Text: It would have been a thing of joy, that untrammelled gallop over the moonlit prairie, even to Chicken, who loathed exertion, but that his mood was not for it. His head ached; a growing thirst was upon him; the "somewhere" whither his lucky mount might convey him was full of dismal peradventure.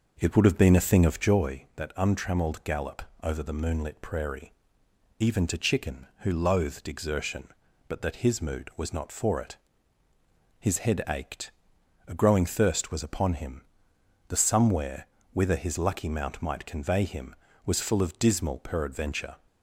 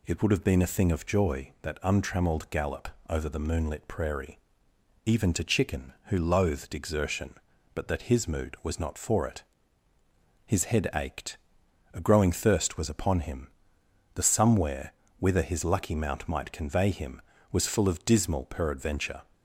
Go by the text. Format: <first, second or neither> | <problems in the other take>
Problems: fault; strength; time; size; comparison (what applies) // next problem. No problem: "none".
second | starts louder than the rest; noticeable; until 1.4 s; 5.5 dB // pauses between "gallop" and "over"; slight; at 3.0 s; 0.18 s long; slight in the second // pauses between "somewhere" and "whither"; slight; at 15.0 s; 0.28 s long; slight in the second